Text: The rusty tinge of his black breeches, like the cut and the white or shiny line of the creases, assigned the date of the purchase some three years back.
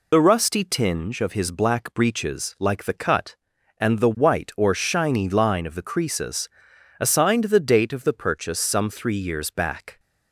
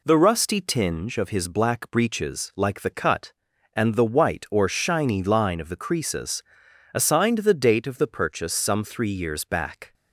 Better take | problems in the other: second | loses the start of "The"; at 0.1 s; 50 ms

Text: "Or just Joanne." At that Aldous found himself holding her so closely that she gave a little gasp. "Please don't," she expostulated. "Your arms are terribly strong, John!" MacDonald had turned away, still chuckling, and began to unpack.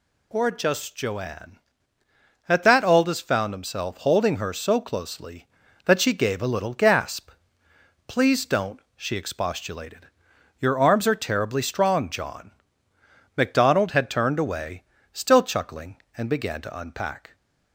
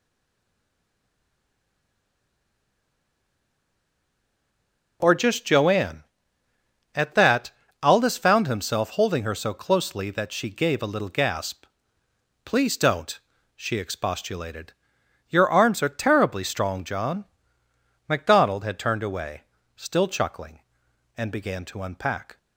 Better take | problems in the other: first | stays silent before the first word; strong; until 5.0 s; 5.0 s long // pauses between "that" and "Aldous"; slight; at 7.4 s; 0.32 s long

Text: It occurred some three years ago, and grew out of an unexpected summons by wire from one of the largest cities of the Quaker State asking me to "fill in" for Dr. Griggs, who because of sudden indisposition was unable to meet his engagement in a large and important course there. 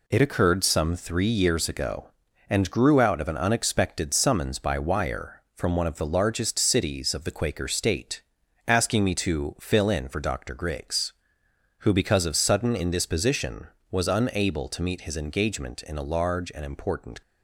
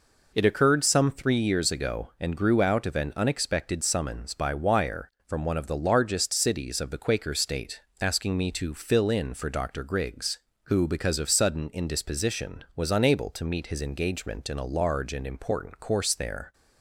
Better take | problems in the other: second | pauses between "State" and "asking"; noticeable; at 8.2 s; 0.46 s long; slight in the second // stops before "course there"; at 17.2 s

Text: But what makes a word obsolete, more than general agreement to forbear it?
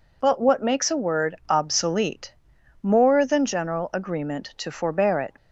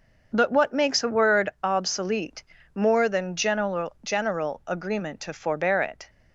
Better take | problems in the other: first | starts louder than the rest; until 1.3 s; 6.5 dB // says "general" twice; at 4.0 s

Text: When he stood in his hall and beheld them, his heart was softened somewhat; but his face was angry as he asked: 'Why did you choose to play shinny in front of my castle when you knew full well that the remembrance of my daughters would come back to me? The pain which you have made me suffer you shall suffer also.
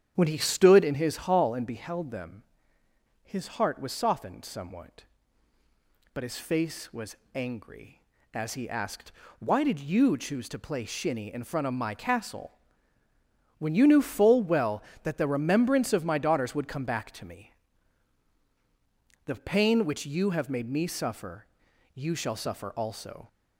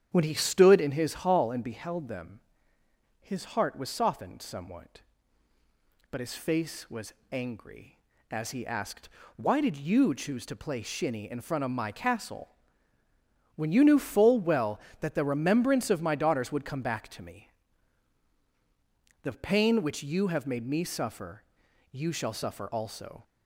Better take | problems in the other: neither | starts louder than the rest; strong; the same in both // pauses between "was" and "angry"; slight; the same in both // pauses between "castle" and "when"; the same in both // pauses between "suffer" and "you"; noticeable; the same in both

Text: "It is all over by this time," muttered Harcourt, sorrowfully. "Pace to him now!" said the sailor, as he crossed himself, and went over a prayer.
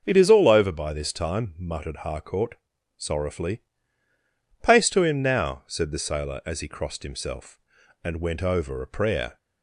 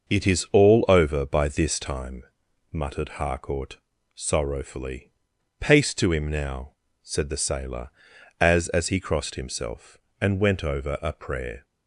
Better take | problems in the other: first | starts louder than the rest; noticeable; until 1.1 s; 6 dB; noticeable in the first // says "as" twice; at 8.6 s

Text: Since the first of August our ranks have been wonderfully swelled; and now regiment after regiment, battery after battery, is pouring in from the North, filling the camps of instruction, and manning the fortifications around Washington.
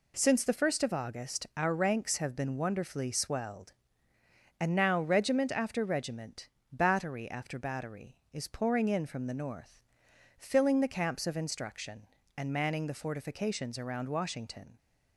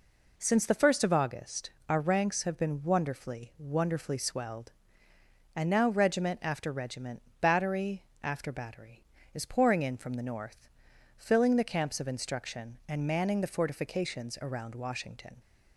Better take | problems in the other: first | pauses between "August" and "our"; slight; at 1.6 s; 0.18 s long // says "wonderfully" twice; at 3.5 s // pauses between "battery" and "after"; slight; at 8.0 s; 0.18 s long

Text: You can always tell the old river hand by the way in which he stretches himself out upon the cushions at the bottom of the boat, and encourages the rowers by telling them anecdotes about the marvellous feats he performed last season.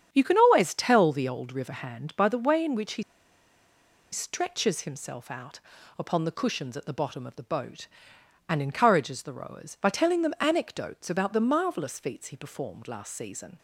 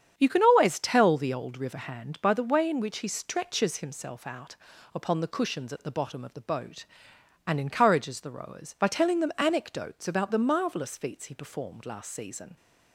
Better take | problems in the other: second | starts louder than the rest; strong; until 1.1 s; 8 dB; strong in the second // pauses between "he" and "stretches"; at 3.0 s; 1.0 s long // pauses between "out" and "upon"; at 5.5 s; 0.38 s long; also in the second

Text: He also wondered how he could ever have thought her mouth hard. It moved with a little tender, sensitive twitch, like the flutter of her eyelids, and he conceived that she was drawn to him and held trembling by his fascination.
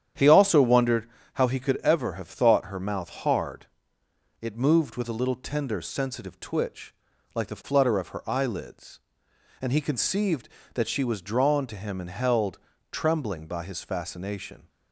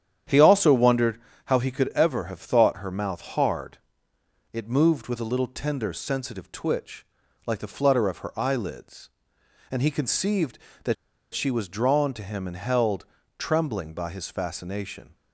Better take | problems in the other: first | starts louder than the rest; strong; until 1.5 s; 9.5 dB; strong in the first // pauses between "wondered" and "how"; slight; at 1.1 s; 0.28 s long; slight in the first // pauses between "that" and "she"; at 10.9 s; 0.39 s long // pauses between "held" and "trembling"; slight; at 13.0 s; 0.32 s long; slight in the first

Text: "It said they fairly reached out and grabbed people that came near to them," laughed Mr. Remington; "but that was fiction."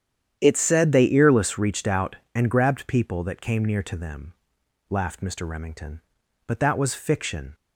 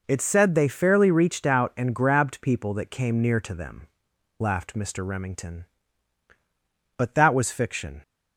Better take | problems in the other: second | starts louder than the rest; strong; until 1.4 s; 9.5 dB // says "earless" for "fairly"; at 1.0 s

